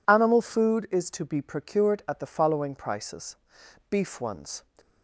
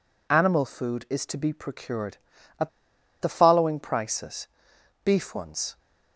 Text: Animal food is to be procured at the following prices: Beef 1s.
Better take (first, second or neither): first